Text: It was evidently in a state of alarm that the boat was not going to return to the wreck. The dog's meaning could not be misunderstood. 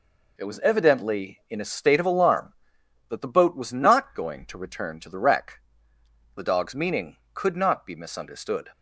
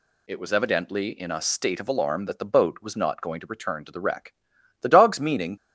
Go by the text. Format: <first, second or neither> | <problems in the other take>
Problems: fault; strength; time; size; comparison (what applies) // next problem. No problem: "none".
first | stops before "could not be misunderstood"; at 5.5 s